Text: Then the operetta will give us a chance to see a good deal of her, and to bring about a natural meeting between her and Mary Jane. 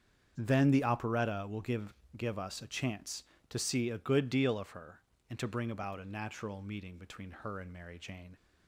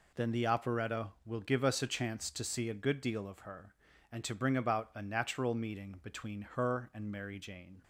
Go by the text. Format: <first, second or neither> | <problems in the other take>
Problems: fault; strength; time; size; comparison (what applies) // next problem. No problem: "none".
second | starts louder than the rest; strong; until 1.3 s; 7.5 dB // says "give" twice; at 2.1 s